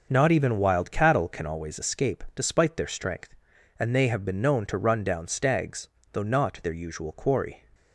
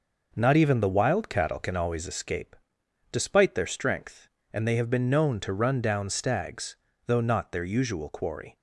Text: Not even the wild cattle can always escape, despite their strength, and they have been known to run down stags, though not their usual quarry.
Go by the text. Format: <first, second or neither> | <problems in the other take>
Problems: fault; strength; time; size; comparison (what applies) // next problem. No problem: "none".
second | starts louder than the rest; until 1.1 s; 6 dB // skips "the"; at 0.5 s